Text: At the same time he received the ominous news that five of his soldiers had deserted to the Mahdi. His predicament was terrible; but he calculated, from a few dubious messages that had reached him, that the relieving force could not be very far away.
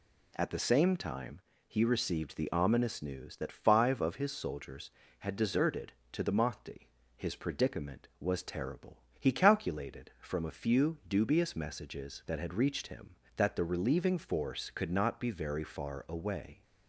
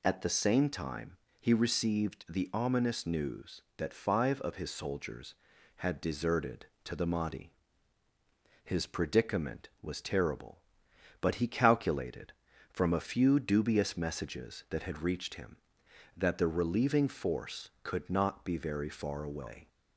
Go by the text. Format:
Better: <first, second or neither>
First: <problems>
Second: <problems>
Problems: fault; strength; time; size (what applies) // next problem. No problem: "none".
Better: second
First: pauses between "time" and "he"; slight; at 1.3 s; 0.28 s long // skips "but"; at 9.0 s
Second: pauses between "time" and "he"; slight; at 1.1 s; 0.22 s long